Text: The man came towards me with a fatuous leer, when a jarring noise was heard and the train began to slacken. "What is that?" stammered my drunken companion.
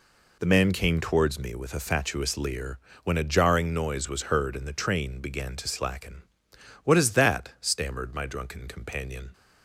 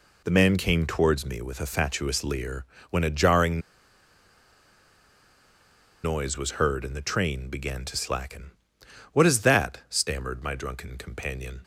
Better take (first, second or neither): first